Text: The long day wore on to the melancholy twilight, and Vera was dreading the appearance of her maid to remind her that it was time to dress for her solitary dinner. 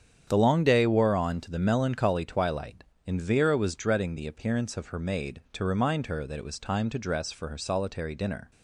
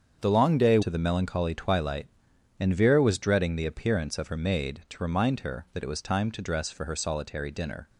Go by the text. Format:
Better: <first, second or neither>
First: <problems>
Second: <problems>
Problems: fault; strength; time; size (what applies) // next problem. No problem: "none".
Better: first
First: starts louder than the rest; strong; until 1.2 s; 8.5 dB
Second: starts louder than the rest; strong; until 1.2 s; 7.5 dB // skips "wore on"; at 0.8 s